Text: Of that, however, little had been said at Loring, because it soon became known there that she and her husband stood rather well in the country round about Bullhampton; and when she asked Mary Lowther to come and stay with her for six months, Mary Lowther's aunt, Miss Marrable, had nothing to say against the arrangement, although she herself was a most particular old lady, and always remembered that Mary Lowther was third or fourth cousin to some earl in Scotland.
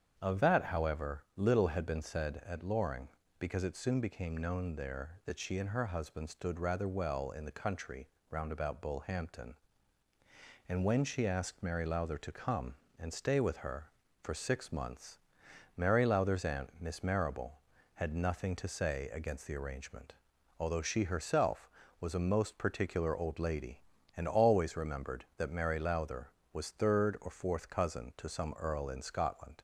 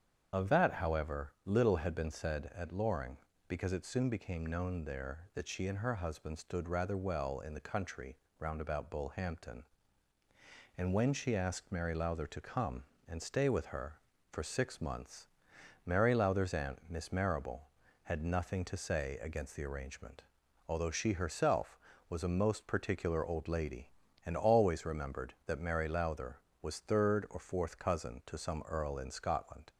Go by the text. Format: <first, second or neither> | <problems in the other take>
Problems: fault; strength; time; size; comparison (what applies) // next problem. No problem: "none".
first | loses the start of "Of"; at 0.3 s; 55 ms // starts louder than the rest; strong; until 1.3 s; 8 dB; strong in the first // pauses between "country" and "round"; slight; at 8.1 s; 0.24 s long; slight in the first